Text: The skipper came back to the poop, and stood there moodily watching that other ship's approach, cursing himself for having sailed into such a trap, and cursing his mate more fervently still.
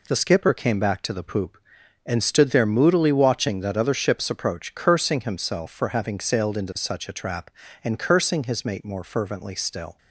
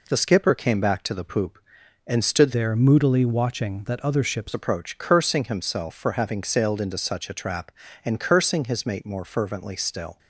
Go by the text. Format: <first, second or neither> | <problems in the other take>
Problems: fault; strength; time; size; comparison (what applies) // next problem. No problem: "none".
first | changes voice from "there" to "ship's"; from 2.5 to 4.5 s; 2.0 s long